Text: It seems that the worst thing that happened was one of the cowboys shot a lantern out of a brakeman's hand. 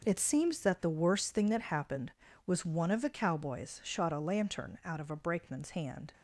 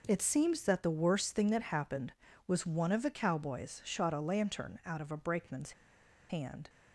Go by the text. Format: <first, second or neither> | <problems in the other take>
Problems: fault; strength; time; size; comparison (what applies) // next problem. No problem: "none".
first | pauses between "brakeman's" and "hand"; noticeable; at 5.7 s; 0.58 s long